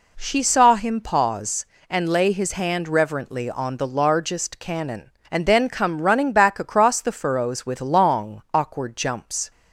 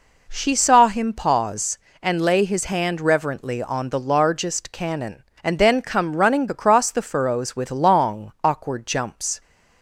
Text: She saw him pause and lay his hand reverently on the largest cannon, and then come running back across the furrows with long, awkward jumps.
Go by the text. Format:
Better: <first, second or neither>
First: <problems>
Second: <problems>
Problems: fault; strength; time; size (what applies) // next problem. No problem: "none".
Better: first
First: none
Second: skips "back"; at 6.4 s